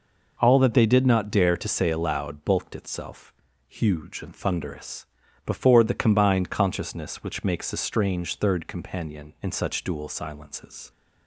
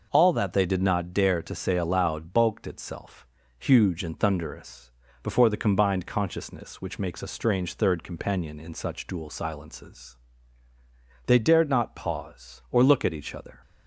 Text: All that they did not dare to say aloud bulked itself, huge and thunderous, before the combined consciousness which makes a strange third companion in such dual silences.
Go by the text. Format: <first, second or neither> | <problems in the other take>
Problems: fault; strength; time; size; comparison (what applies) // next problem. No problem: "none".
first | goes on to say "They dared not pause or look at each other"; strong; from 11.2 s on; 2.3 s long